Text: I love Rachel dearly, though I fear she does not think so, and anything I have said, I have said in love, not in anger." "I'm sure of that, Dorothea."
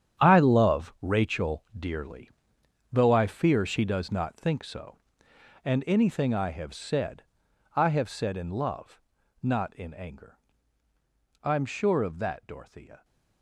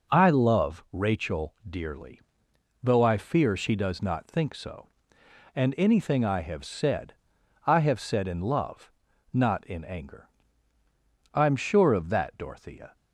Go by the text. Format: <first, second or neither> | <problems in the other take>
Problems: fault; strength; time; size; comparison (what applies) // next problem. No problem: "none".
second | gets quieter; strong; throughout; 12.5 dB // pauses between "Rachel" and "dearly"; slight; at 1.6 s; 0.16 s long; slight in the second